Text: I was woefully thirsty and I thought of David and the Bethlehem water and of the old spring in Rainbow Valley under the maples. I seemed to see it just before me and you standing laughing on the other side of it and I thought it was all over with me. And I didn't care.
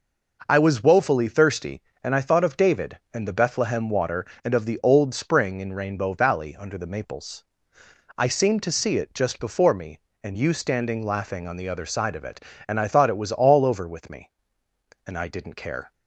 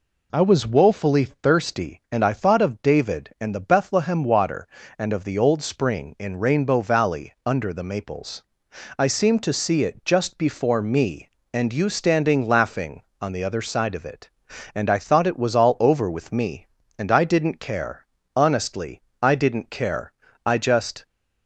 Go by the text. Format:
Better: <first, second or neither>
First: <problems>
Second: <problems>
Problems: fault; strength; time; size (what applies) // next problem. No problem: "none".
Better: first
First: none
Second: goes on to say "Honestly I didn't care I just"; strong; from 18.3 s on; 2.7 s long